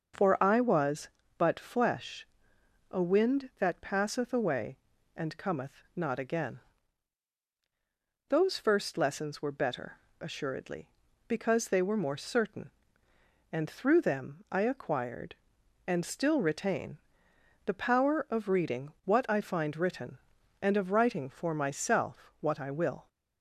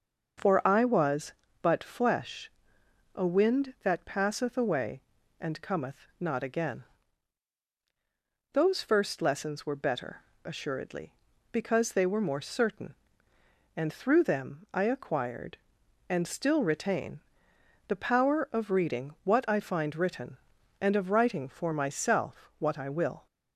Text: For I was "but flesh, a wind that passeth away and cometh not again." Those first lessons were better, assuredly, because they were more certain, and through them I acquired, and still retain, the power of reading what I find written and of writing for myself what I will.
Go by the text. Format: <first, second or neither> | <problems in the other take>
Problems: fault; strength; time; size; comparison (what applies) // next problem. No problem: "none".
neither | starts louder than the rest; the same in both